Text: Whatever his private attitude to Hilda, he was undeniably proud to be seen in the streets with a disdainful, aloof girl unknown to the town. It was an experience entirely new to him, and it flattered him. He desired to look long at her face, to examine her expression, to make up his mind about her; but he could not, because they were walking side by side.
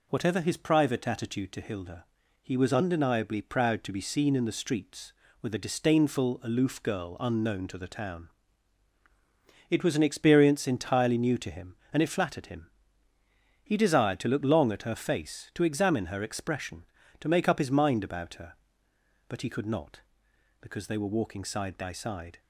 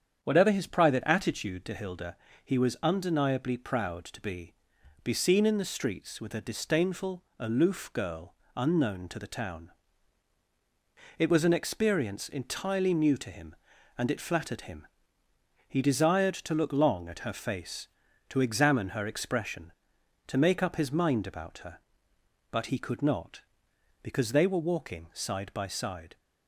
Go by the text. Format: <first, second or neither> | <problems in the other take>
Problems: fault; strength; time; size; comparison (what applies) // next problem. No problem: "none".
first | starts louder than the rest; strong; until 1.2 s; 8 dB // says "be" twice; at 5.0 s // pauses between "girl" and "unknown"; slight; at 8.3 s; 0.20 s long